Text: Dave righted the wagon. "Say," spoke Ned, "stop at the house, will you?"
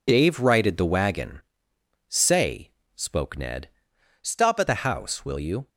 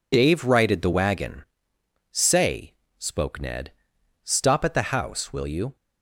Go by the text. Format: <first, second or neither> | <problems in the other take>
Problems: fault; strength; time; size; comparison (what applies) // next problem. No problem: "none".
second | changes voice from "stop" to "at"; from 4.2 to 4.6 s; 0.4 s long